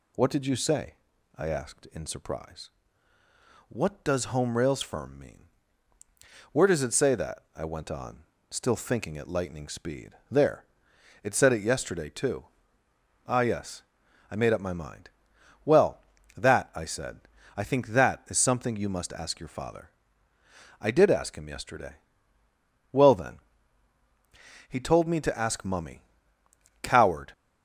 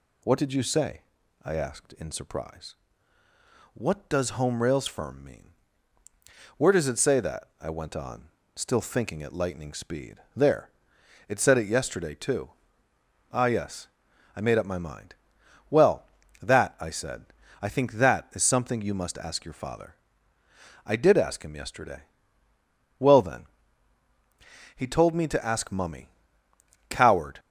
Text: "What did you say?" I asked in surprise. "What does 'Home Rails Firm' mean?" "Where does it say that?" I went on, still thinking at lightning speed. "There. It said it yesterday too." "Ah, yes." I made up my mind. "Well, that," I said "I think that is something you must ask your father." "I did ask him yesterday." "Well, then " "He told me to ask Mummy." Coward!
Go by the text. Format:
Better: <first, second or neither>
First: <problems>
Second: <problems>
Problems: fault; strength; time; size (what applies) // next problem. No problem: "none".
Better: neither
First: pauses between "said" and "I"; slight; at 17.1 s; 0.36 s long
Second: pauses between "said" and "I"; slight; at 17.2 s; 0.36 s long